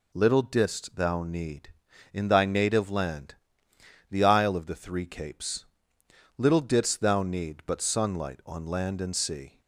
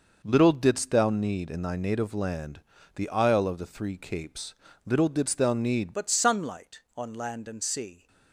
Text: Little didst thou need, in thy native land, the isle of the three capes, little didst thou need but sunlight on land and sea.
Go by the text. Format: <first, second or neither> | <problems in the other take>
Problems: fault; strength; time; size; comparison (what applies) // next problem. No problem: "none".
first | changes voice at "but"; from 5.9 s on; 2.1 s long